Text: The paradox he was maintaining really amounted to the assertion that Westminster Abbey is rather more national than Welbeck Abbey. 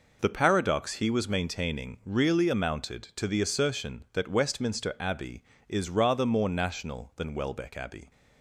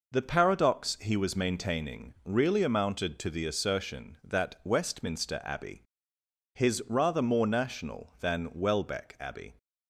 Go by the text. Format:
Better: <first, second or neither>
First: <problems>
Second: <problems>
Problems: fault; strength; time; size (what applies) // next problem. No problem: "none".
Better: first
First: none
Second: says "his" for "is"; at 6.5 s